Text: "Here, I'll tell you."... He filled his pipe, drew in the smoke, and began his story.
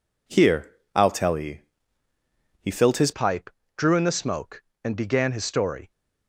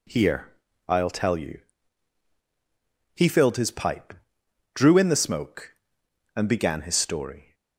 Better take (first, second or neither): second